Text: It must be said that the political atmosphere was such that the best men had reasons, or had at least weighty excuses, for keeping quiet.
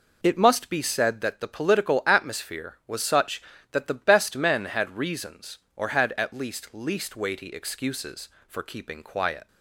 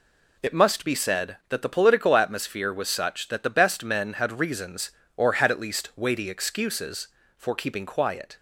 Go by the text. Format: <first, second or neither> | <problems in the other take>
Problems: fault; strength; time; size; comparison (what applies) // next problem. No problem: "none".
second | says "least" twice; at 6.7 s